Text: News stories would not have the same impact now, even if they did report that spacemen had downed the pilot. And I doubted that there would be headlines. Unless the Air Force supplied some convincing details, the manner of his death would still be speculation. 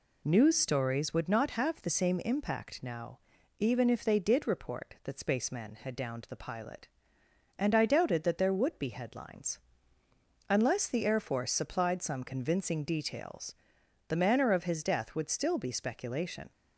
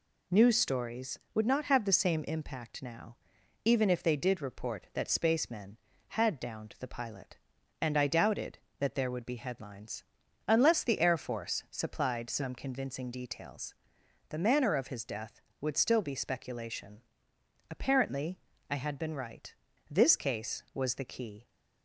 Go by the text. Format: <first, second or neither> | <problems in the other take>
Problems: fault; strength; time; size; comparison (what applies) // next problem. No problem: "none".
first | goes on to say "Apparently I had been right this case was the key"; strong; from 17.7 s on; 3.7 s long